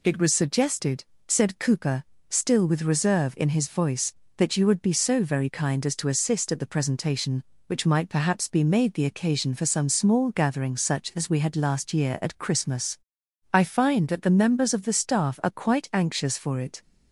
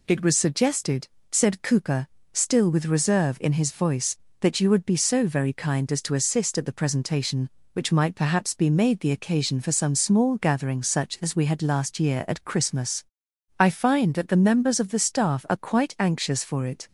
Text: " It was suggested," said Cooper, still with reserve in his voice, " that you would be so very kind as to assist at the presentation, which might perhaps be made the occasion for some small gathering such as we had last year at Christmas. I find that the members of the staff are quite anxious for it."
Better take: neither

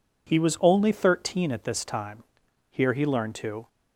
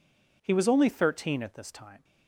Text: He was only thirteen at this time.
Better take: second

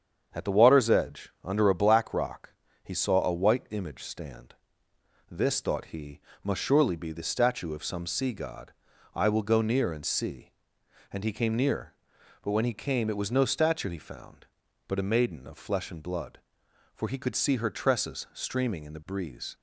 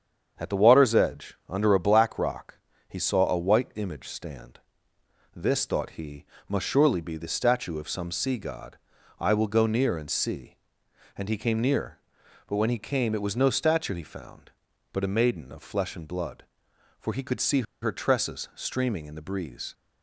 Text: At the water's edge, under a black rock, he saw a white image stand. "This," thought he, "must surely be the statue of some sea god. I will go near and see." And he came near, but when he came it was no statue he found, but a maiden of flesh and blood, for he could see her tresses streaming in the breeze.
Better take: first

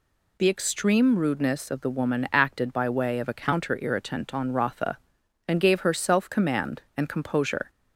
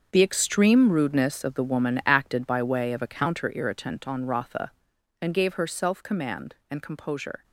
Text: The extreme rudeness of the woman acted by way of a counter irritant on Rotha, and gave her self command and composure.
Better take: first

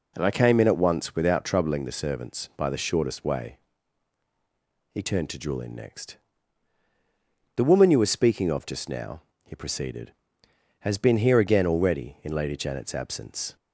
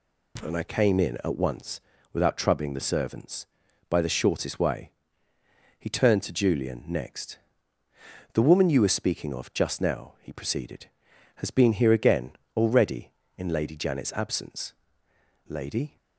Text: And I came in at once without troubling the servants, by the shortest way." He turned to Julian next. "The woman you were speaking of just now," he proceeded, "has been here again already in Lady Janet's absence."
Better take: first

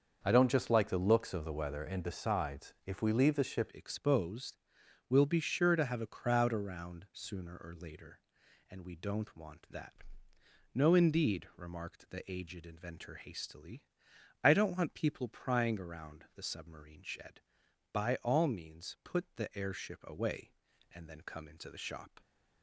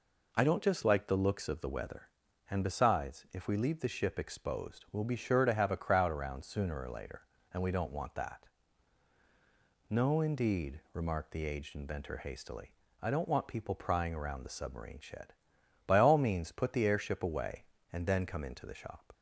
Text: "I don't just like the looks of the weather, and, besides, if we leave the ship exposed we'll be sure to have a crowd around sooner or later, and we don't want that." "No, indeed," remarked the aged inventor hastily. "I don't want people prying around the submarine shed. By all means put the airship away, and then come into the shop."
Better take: second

